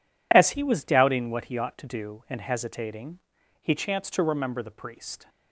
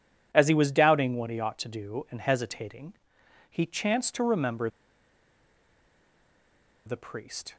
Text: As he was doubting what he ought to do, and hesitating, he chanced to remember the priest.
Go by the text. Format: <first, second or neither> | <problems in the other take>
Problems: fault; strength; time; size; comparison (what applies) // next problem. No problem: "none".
first | pauses between "remember" and "the"; strong; at 4.6 s; 2.1 s long